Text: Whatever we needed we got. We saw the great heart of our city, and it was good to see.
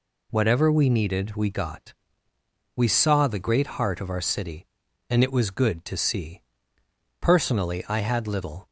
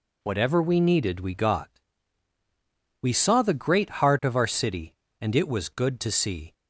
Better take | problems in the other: second | goes on to say "Personally I had little"; noticeable; from 7.4 s on; 1.2 s long

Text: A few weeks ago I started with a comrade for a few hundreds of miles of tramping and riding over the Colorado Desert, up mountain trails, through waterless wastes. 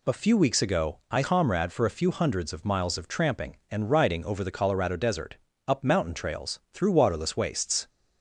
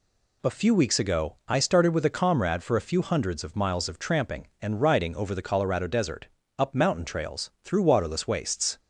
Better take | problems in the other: second | skips "started with a"; at 1.2 s

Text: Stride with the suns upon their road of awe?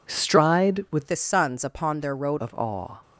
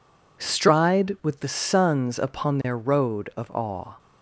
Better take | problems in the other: second | changes voice from "the" to "road"; from 1.0 to 2.3 s; 1.3 s long

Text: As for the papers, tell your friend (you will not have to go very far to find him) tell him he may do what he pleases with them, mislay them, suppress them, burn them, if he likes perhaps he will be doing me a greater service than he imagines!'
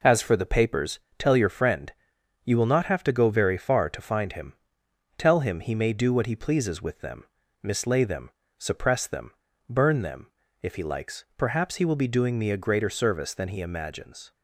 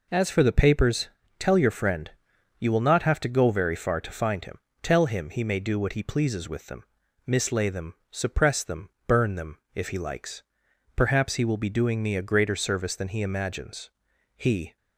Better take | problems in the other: first | pauses between "likes" and "perhaps"; noticeable; at 10.4 s; 0.50 s long // goes on to say "He"; slight; from 14.3 s on; 0.40 s long

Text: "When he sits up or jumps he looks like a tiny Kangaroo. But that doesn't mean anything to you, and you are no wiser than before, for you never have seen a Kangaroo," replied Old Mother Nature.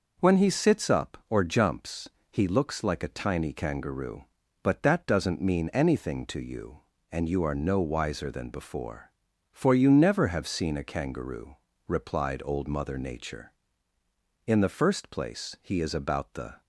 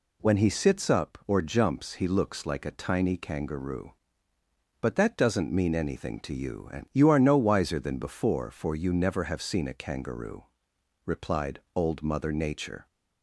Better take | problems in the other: second | pauses between "jumps" and "he"; slight; at 2.0 s; 0.24 s long // goes on to say "In the first place he is about the"; strong; from 14.4 s on; 2.1 s long

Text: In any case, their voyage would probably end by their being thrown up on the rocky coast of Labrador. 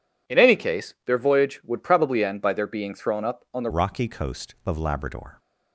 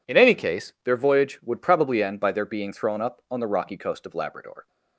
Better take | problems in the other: second | changes voice at "rocky"; from 3.7 s on; 1.6 s long

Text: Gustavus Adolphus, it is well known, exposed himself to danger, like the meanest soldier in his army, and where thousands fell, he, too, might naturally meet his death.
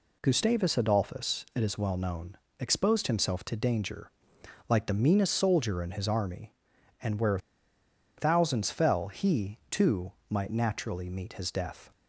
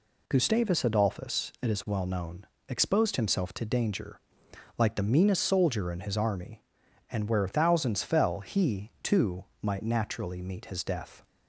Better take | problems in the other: second | pauses between "where" and "thousands"; noticeable; at 7.3 s; 0.78 s long

